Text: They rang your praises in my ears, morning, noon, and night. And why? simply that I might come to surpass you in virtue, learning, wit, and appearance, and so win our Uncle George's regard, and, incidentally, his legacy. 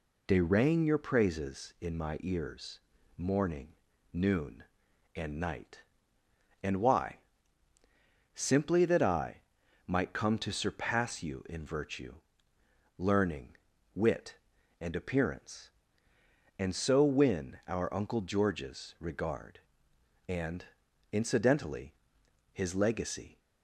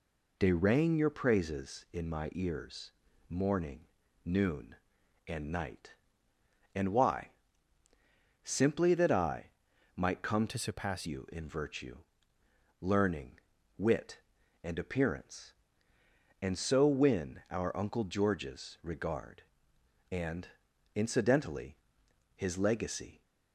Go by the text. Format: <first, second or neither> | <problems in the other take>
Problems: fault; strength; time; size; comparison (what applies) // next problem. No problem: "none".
first | pauses between "I" and "might"; noticeable; at 9.4 s; 0.48 s long; noticeable in the first // changes voice from "to" to "surpass"; from 10.4 to 11.0 s; 0.6 s long